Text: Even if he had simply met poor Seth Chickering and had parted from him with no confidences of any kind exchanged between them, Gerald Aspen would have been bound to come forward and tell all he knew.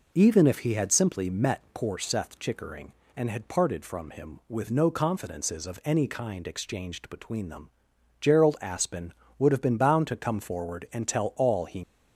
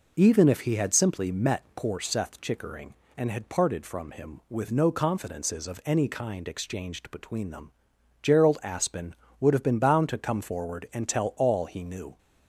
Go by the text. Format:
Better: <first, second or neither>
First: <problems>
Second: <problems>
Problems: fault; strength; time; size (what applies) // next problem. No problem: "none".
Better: second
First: stops before "knew"; at 11.8 s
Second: none